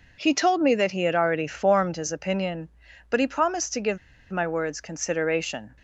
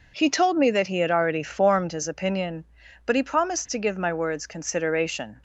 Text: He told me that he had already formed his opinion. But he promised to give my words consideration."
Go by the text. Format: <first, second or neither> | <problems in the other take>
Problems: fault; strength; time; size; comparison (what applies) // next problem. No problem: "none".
second | pauses between "give" and "my"; slight; at 3.9 s; 0.33 s long